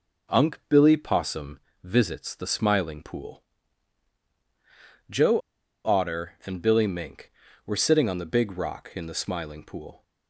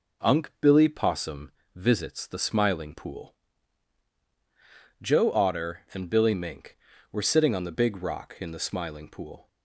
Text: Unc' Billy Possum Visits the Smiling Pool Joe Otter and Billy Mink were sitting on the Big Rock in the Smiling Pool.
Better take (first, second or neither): second